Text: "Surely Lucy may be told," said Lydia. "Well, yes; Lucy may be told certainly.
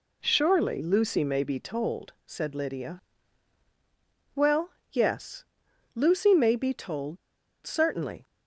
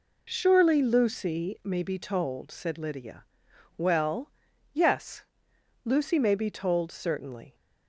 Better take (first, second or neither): second